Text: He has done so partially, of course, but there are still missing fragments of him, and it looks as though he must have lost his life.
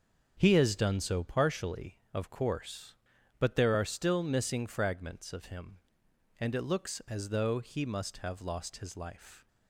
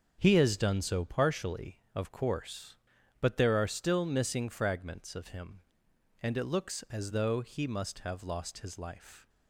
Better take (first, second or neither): neither